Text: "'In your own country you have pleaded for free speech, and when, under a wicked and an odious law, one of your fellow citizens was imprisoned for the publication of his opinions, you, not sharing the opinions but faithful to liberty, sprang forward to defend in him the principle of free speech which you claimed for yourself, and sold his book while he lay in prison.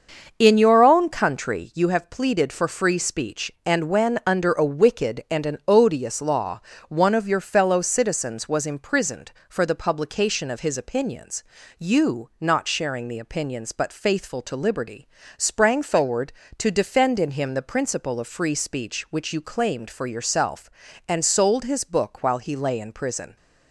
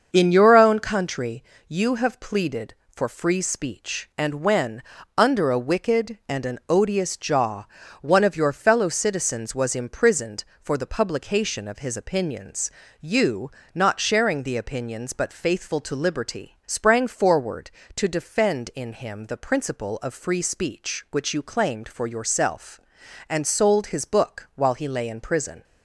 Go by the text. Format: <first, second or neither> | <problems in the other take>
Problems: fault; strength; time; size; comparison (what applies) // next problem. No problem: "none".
first | starts louder than the rest; noticeable; until 1.1 s; 6 dB; also in the first // pauses between "country" and "you"; slight; at 1.4 s; 0.28 s long // says "jaw" for "law"; at 7.1 s